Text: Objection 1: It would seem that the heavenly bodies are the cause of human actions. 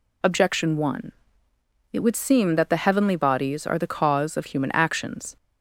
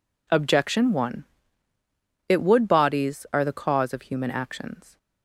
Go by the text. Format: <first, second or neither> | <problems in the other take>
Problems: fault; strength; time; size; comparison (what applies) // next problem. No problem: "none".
first | skips "seem that the heavenly"; at 2.6 s